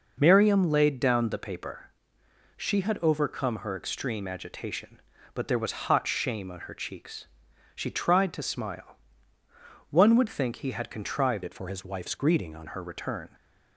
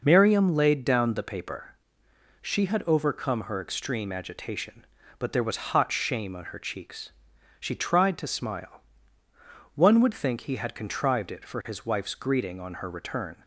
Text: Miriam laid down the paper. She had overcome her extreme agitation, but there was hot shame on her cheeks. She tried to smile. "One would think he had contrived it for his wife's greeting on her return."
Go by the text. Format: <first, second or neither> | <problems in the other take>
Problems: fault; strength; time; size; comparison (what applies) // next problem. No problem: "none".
second | changes voice from "it" to "on"; from 11.4 to 12.6 s; 1.2 s long